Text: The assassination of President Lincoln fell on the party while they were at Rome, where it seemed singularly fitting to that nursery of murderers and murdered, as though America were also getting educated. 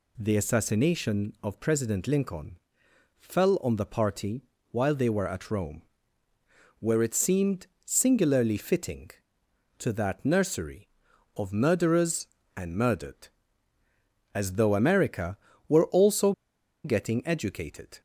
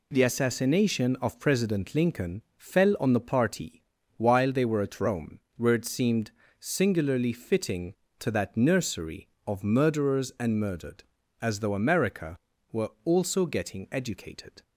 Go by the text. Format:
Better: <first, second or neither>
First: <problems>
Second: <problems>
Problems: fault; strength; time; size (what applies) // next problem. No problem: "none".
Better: second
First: pauses between "Lincoln" and "fell"; noticeable; at 2.5 s; 0.62 s long // pauses between "party" and "while"; slight; at 4.4 s; 0.30 s long // pauses between "seemed" and "singularly"; slight; at 7.6 s; 0.18 s long // pauses between "also" and "getting"; noticeable; at 16.3 s; 0.52 s long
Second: pauses between "Lincoln" and "fell"; slight; at 2.4 s; 0.16 s long // pauses between "party" and "while"; slight; at 3.8 s; 0.36 s long // pauses between "seemed" and "singularly"; slight; at 6.3 s; 0.28 s long